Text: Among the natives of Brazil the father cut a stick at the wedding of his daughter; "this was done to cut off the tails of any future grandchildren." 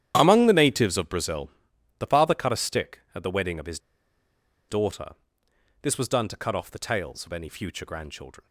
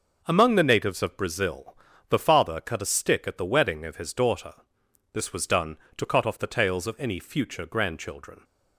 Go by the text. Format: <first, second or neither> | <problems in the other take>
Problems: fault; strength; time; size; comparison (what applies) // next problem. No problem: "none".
second | starts louder than the rest; strong; until 1.1 s; 10.5 dB // pauses between "Brazil" and "the"; noticeable; at 1.4 s; 0.48 s long; slight in the second // pauses between "his" and "daughter"; noticeable; at 3.7 s; 0.90 s long